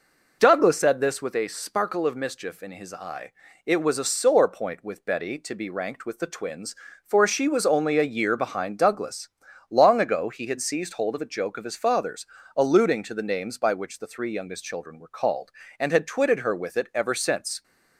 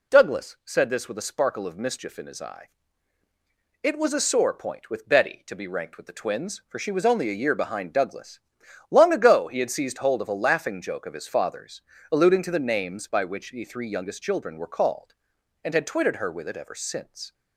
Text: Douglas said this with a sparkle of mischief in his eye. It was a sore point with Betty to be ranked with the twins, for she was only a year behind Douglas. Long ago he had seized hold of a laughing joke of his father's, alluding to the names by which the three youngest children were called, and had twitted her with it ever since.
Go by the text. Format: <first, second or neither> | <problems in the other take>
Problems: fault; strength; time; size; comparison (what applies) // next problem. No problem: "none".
second | skips "laughing"; at 11.3 s